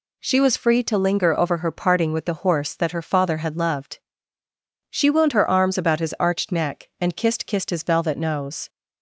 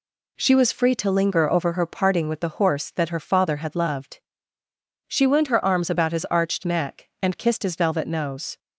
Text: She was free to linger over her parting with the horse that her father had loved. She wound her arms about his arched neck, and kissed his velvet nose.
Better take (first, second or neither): second